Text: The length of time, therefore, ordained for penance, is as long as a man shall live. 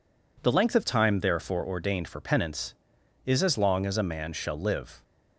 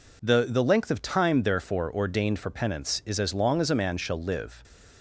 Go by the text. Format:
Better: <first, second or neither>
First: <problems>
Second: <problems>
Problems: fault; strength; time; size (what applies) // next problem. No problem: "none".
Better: first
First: none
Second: says "The" twice; at 0.4 s // stays silent after the last word; slight; from 4.4 s on; 0.6 s long